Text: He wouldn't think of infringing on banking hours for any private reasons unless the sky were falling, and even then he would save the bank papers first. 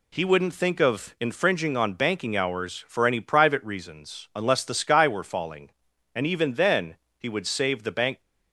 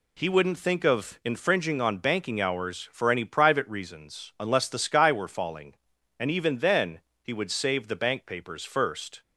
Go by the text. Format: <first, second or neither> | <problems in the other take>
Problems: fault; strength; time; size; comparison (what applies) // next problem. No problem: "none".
second | pauses between "then" and "he"; slight; at 6.9 s; 0.20 s long; slight in the second // stops before "papers first"; at 8.2 s